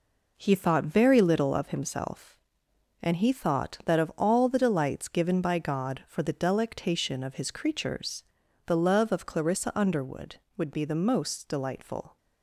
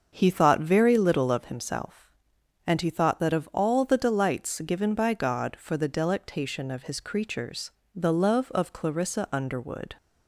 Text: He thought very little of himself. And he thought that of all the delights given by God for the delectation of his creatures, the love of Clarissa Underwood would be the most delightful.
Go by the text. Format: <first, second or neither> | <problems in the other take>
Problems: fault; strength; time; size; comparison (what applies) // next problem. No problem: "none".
first | starts louder than the rest; until 1.1 s; 6.5 dB // stops before "would be the most delightful"; at 9.9 s